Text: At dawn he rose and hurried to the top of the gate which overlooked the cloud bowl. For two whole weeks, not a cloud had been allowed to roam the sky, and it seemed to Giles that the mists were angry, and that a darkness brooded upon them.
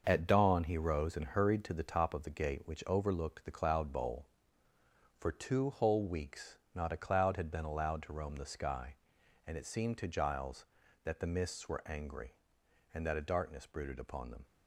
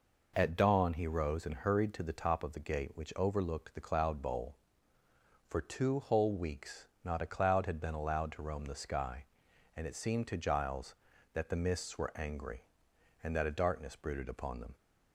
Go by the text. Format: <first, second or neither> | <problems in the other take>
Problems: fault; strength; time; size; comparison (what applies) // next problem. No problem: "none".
second | gets quieter; throughout; 7 dB